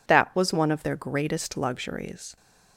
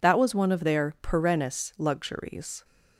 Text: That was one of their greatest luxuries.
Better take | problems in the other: first | says "perennis" for "greatest"; at 1.0 s

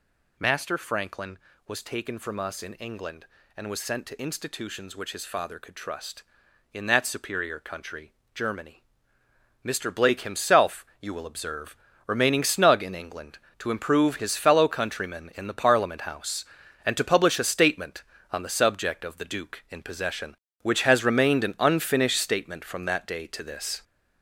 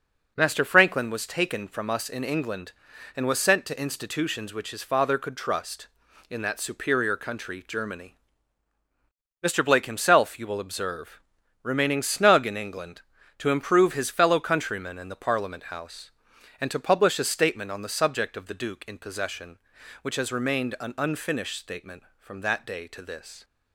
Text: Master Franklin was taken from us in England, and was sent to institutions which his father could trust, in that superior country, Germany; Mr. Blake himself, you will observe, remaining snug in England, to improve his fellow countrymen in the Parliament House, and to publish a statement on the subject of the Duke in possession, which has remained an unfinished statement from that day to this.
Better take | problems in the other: second | gets louder; noticeable; throughout; 5 dB

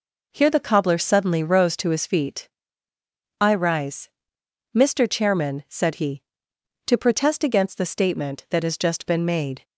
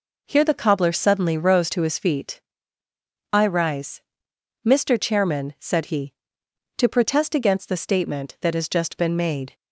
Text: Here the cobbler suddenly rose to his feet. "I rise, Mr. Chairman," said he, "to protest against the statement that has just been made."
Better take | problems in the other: neither | none

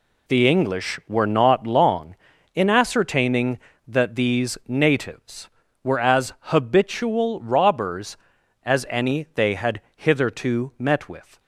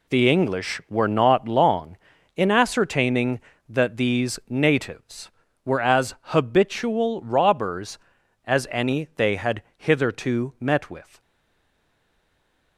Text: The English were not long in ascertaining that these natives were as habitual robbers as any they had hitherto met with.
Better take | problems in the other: first | pauses between "had" and "hitherto"; slight; at 9.6 s; 0.16 s long; slight in the first // stays silent after the last word; noticeable; from 11.2 s on; 1.5 s long

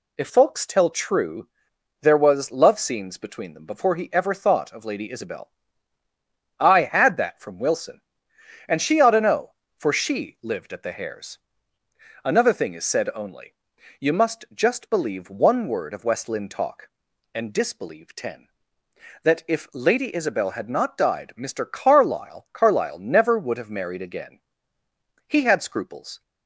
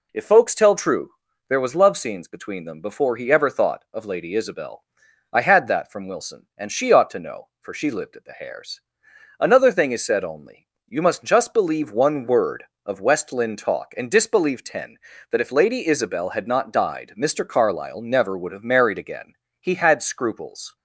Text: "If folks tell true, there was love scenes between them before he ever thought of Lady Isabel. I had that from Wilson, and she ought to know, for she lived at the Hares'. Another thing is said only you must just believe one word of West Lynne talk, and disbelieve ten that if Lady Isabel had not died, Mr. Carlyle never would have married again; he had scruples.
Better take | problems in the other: second | pauses between "only" and "you"; noticeable; at 13.5 s; 0.48 s long; slight in the second // says "Carlyle" twice; at 22.5 s

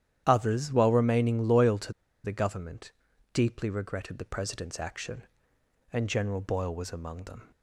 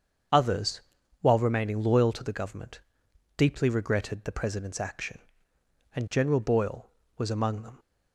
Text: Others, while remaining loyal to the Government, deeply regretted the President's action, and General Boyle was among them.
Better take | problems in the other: second | starts louder than the rest; strong; until 1.2 s; 10.5 dB; strong in the second // pauses between "to" and "the"; slight; at 1.9 s; 0.32 s long

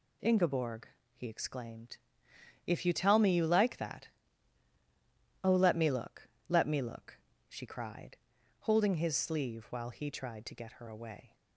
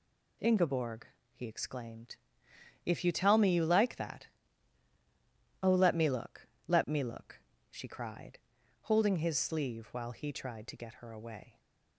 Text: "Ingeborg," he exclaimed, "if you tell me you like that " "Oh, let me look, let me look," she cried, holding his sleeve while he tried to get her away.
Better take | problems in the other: neither | none

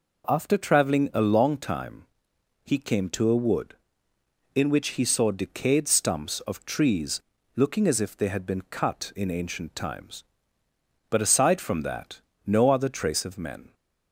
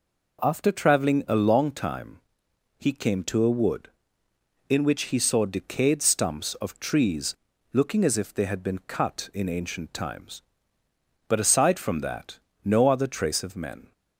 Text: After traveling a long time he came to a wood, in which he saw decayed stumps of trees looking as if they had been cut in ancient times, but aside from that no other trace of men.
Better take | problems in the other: neither | pauses between "time" and "he"; noticeable; the same in both // pauses between "trees" and "looking"; the same in both // pauses between "that" and "no"; slight; the same in both

